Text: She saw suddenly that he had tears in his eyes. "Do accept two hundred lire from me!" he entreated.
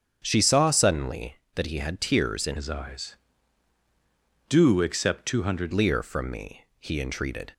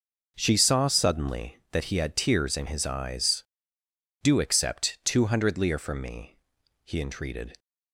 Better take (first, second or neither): second